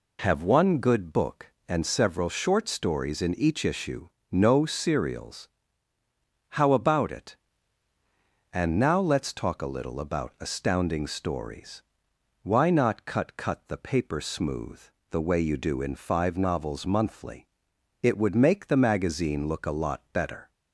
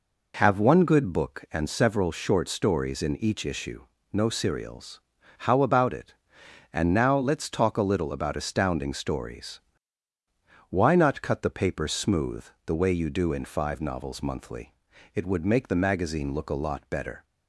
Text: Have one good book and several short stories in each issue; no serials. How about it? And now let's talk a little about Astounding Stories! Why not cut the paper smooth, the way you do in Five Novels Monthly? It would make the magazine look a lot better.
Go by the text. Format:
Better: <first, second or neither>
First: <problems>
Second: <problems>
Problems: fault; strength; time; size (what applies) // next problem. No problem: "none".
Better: second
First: says "cut" twice; at 13.3 s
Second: none